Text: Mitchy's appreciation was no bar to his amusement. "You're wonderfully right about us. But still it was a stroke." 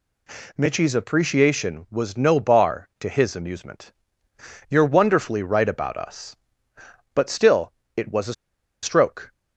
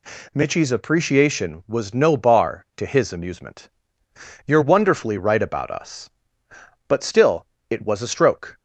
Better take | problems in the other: second | pauses between "still" and "it"; slight; at 7.7 s; 0.24 s long; slight in the second // pauses between "a" and "stroke"; noticeable; at 8.3 s; 0.49 s long

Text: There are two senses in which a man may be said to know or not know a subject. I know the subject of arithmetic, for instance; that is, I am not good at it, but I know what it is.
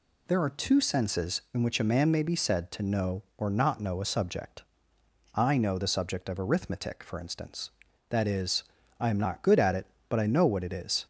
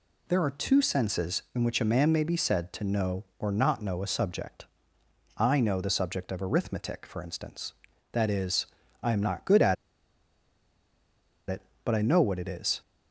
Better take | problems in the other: first | pauses between "at" and "it"; strong; at 9.7 s; 1.7 s long

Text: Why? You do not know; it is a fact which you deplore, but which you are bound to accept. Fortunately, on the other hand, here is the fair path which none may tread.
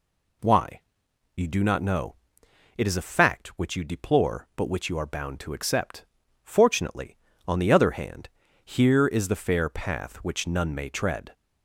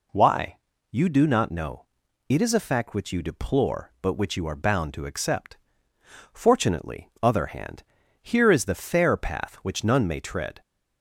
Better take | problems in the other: first | skips "on the"; at 7.1 s

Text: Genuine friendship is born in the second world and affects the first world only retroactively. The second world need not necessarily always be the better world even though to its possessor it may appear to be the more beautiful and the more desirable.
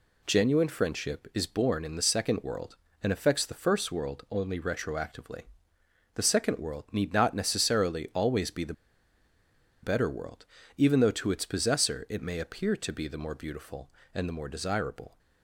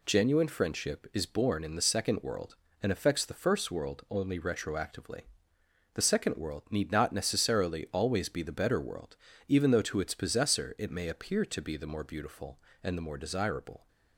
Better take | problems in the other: second | pauses between "the" and "better"; at 8.7 s; 1.0 s long // pauses between "world" and "even"; slight; at 10.4 s; 0.32 s long; slight in the second

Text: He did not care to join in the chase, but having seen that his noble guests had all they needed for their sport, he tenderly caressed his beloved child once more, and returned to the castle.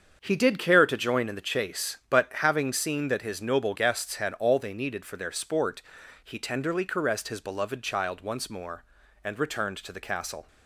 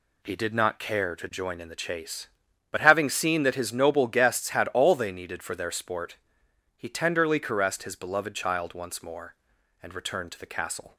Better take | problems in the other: second | starts louder than the rest; strong; until 1.2 s; 7 dB // skips "not"; at 0.5 s

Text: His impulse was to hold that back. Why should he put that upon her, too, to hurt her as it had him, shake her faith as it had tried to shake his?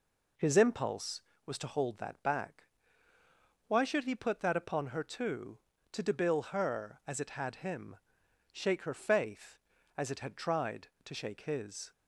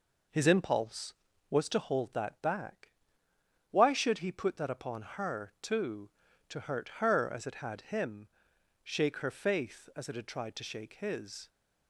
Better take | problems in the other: second | says "debil" for "hurt"; at 6.0 s

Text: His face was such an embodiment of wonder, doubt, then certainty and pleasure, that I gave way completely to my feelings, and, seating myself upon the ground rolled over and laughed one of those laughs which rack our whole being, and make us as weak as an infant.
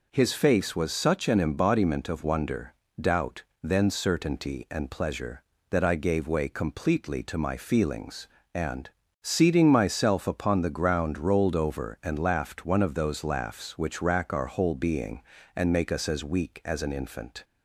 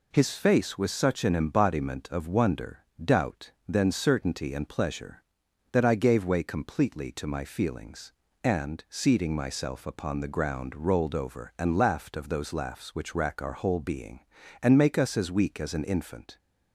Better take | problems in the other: first | skips "one"; at 12.1 s

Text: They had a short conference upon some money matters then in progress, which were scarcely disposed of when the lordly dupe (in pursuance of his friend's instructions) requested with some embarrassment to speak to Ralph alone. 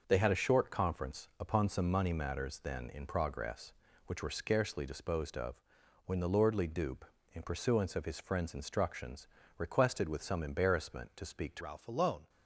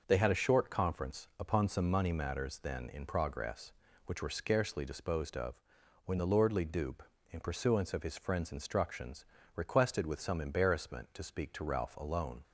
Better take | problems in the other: second | starts louder than the rest; noticeable; until 1.0 s; 6 dB // pauses between "of" and "when"; noticeable; at 5.5 s; 0.50 s long; noticeable in the second // changes voice at "Ralph"; from 11.5 s on; 0.7 s long

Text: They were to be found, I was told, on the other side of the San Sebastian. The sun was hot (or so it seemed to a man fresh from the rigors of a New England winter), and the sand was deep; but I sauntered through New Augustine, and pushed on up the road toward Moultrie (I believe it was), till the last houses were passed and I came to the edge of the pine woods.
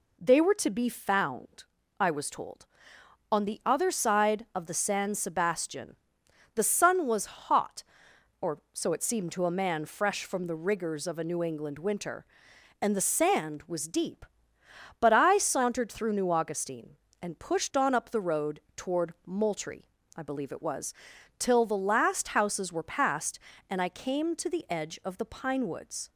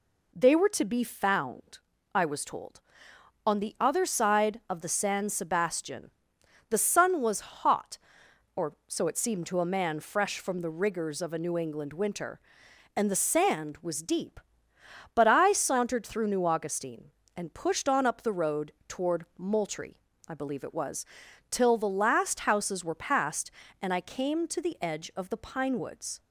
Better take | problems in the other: neither | none

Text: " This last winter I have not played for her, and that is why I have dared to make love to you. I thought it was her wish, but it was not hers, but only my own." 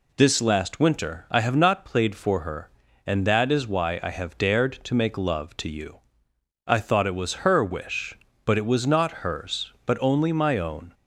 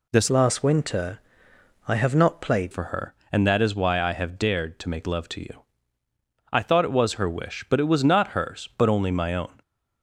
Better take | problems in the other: first | changes voice from "last" to "played"; from 0.2 to 2.7 s; 2.5 s long // pauses between "winter" and "I"; noticeable; at 1.1 s; 0.68 s long

